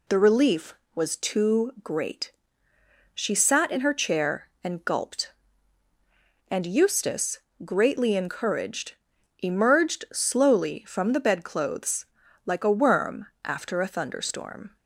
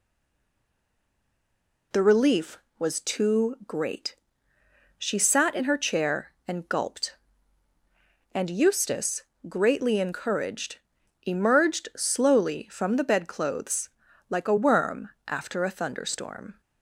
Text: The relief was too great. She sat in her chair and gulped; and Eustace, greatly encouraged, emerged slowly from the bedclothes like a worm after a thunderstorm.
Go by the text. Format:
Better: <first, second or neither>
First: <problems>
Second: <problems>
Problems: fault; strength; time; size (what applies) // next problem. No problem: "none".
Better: first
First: pauses between "bedclothes" and "like"; at 12.0 s; 0.40 s long // pauses between "worm" and "after"; slight; at 13.2 s; 0.16 s long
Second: stays silent before the first word; noticeable; until 1.9 s; 1.9 s long // pauses between "bedclothes" and "like"; at 13.8 s; 0.40 s long // pauses between "worm" and "after"; slight; at 15.0 s; 0.16 s long